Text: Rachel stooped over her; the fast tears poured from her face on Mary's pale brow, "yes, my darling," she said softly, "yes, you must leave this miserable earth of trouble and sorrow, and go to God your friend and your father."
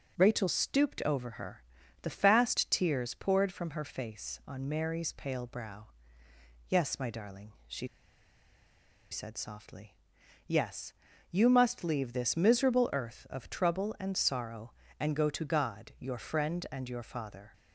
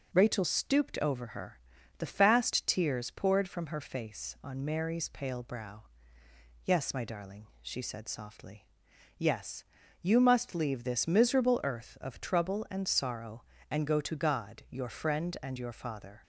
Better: second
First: pauses between "she" and "said"; strong; at 7.8 s; 1.2 s long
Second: none

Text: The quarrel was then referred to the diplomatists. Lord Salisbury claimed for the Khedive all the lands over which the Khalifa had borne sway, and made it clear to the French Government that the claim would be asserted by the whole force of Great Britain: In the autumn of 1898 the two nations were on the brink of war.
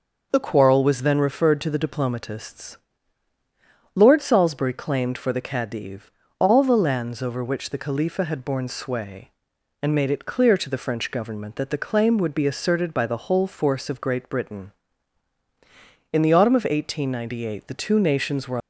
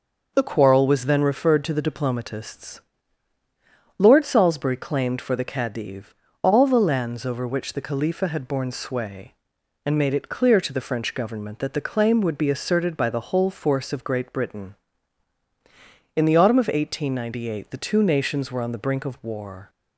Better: second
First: starts louder than the rest; noticeable; until 1.3 s; 6 dB // pauses between "Khedive" and "all"; slight; at 6.1 s; 0.26 s long // stops before "on the brink of war"; at 18.6 s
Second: starts louder than the rest; noticeable; until 1.3 s; 6 dB // pauses between "Khedive" and "all"; slight; at 6.1 s; 0.26 s long

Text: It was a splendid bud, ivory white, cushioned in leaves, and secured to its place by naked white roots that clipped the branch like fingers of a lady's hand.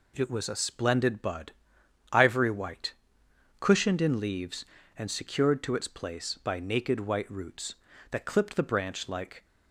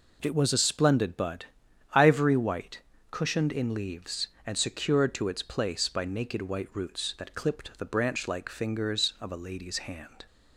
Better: second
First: stops before "fingers of a lady's hand"; at 9.4 s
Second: none

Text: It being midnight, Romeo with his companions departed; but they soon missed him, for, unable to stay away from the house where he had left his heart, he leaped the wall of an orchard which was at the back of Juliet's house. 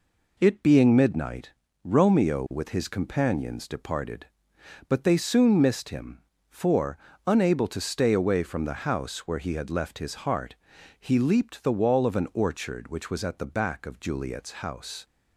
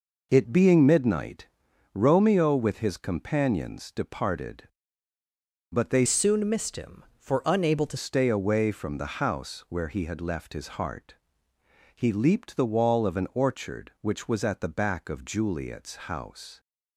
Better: first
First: none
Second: changes voice from "soon" to "to"; from 6.0 to 7.9 s; 1.9 s long

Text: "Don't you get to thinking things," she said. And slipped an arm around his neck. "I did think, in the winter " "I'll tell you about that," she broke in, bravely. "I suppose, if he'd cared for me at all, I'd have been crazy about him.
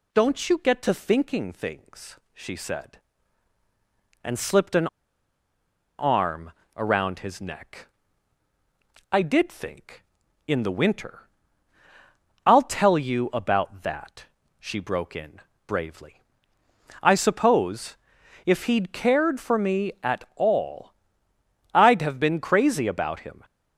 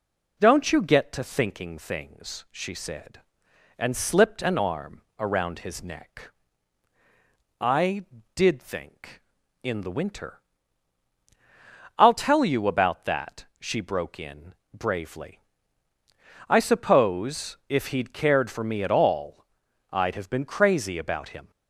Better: second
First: pauses between "an" and "arm"; at 4.8 s; 1.1 s long // pauses between "arm" and "around"; slight; at 6.5 s; 0.24 s long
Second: pauses between "arm" and "around"; slight; at 5.0 s; 0.16 s long

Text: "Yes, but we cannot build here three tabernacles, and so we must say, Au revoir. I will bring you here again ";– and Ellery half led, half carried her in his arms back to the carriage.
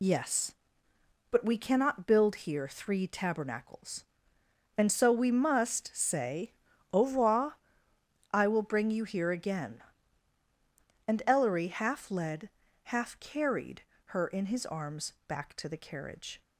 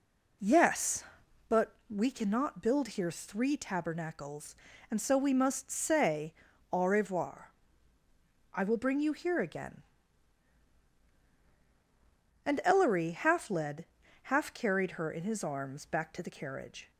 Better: second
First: loses the start of "Yes"; at 0.0 s; 60 ms // pauses between "carried" and "her"; slight; at 13.8 s; 0.34 s long // pauses between "arms" and "back"; slight; at 15.1 s; 0.16 s long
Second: none

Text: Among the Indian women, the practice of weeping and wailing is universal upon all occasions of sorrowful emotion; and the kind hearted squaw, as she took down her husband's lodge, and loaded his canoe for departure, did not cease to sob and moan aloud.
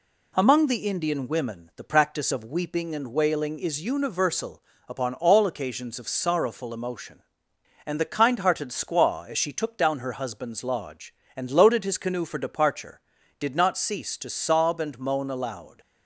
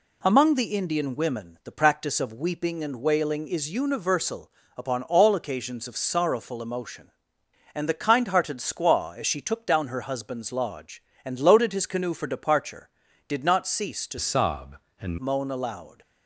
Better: first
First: pauses between "universal" and "upon"; slight; at 4.6 s; 0.26 s long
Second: pauses between "universal" and "upon"; slight; at 4.5 s; 0.26 s long // changes voice from "sob" to "and"; from 14.2 to 15.1 s; 0.9 s long

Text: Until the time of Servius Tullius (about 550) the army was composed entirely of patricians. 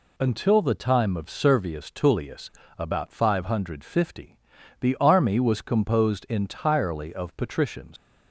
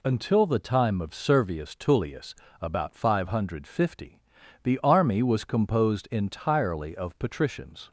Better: second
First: leaves "patricians" unfinished; at 7.9 s; 115 ms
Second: none

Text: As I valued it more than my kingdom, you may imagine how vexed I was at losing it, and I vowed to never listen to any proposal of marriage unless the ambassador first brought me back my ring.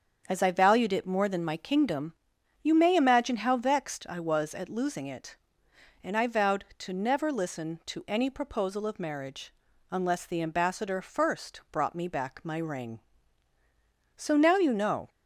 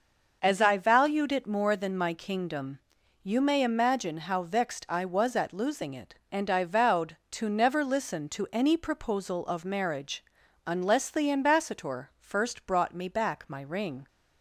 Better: second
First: starts louder than the rest; strong; until 1.2 s; 7 dB // pauses between "marriage" and "unless"; at 9.5 s; 0.38 s long // goes on to say "So now you know"; noticeable; from 14.1 s on; 0.92 s long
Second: starts louder than the rest; noticeable; until 1.4 s; 6 dB // pauses between "marriage" and "unless"; at 10.2 s; 0.44 s long

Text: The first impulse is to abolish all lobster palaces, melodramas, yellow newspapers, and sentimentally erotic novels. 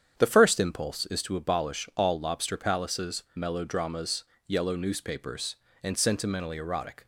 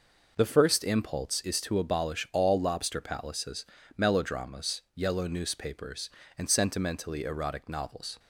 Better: second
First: starts louder than the rest; strong; until 1.2 s; 8.5 dB // stops before "novels"; at 7.0 s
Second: none

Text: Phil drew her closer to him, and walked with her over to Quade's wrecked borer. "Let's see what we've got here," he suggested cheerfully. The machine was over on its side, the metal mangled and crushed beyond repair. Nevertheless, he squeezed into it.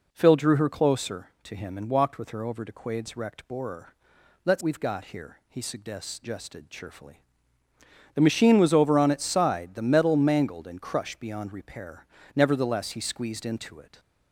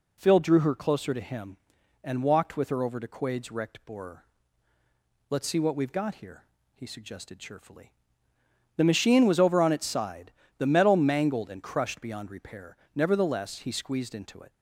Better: second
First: skips "see what"; at 4.6 s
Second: none

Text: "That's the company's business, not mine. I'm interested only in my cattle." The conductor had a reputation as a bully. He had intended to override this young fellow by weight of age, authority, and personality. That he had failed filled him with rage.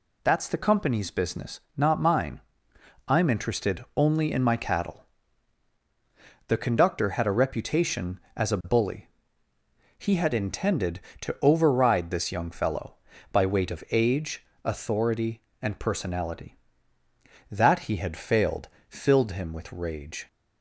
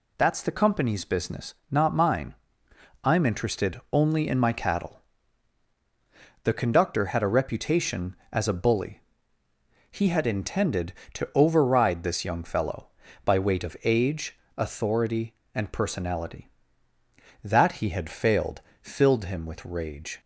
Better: neither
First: pauses between "failed" and "filled"; slight; at 18.6 s; 0.20 s long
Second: pauses between "failed" and "filled"; slight; at 18.6 s; 0.20 s long

